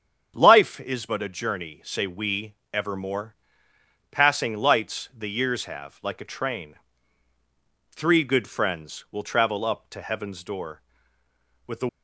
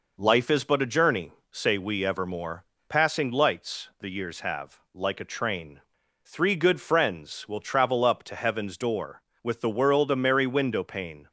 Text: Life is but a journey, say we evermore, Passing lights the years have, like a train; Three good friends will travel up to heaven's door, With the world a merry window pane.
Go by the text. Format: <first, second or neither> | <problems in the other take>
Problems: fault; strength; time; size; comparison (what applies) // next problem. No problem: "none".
second | starts louder than the rest; strong; until 1.3 s; 8 dB // pauses between "we" and "evermore"; slight; at 2.5 s; 0.18 s long // stops before "world a merry window pane"; at 11.8 s